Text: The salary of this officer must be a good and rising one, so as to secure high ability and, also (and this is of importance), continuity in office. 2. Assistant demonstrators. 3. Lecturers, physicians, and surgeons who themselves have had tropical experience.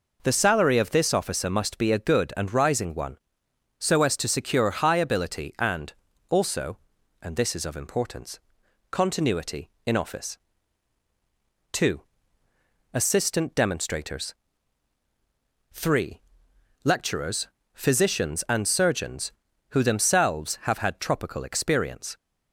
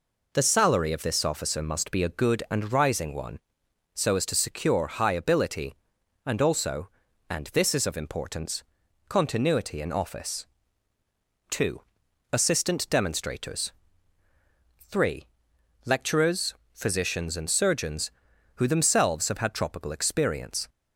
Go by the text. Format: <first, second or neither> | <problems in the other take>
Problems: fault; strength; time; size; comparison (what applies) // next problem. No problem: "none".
neither | none